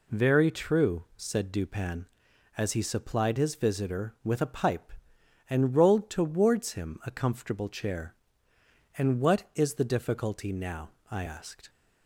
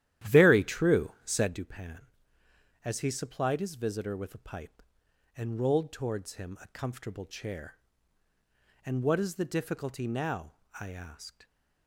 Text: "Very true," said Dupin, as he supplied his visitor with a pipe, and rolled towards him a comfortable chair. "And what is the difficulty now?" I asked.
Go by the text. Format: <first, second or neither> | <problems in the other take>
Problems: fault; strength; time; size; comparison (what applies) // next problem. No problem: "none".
first | starts louder than the rest; strong; until 1.6 s; 12.5 dB